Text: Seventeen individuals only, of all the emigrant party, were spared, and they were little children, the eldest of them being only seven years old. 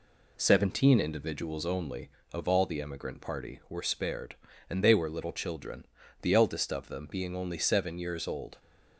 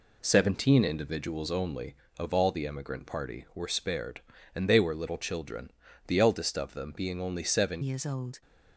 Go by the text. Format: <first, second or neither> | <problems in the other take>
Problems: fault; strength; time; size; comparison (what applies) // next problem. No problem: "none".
first | changes voice at "years"; from 7.8 s on; 0.6 s long